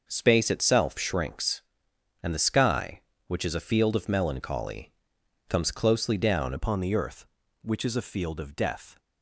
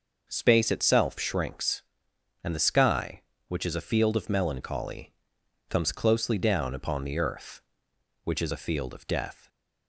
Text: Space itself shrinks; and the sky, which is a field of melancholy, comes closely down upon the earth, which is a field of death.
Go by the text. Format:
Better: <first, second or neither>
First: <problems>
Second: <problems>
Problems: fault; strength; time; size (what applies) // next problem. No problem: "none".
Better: second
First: starts louder than the rest; until 1.0 s; 6 dB // changes voice at "upon"; from 6.5 s on; 2.4 s long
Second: none